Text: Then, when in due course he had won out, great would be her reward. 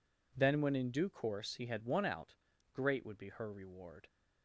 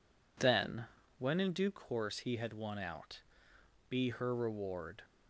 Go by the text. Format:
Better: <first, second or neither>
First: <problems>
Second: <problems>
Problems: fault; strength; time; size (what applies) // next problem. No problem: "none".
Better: first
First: none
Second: skips "great would"; at 3.5 s